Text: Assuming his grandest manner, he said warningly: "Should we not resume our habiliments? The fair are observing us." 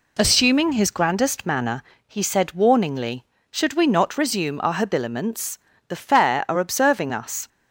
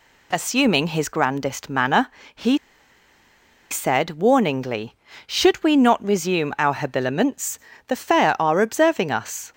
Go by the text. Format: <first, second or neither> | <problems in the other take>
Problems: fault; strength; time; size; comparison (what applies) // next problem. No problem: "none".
first | pauses between "he" and "said"; at 2.5 s; 1.1 s long